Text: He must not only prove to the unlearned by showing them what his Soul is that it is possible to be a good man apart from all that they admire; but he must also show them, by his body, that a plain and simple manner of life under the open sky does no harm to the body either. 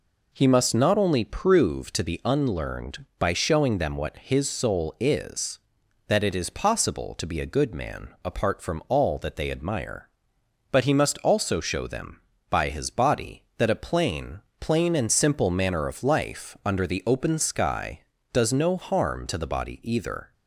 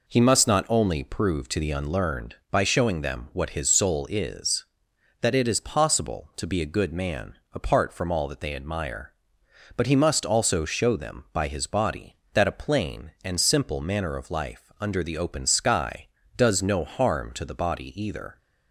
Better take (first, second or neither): second